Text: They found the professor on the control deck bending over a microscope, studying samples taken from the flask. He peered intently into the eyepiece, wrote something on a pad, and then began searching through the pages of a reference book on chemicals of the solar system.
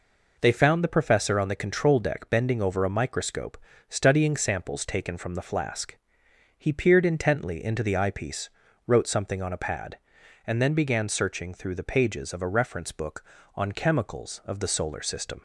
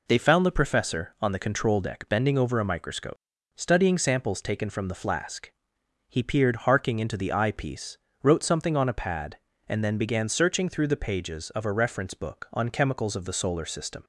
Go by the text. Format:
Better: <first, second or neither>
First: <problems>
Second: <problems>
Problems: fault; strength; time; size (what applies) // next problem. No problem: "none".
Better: first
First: none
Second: says "harking" for "intently"; at 6.5 s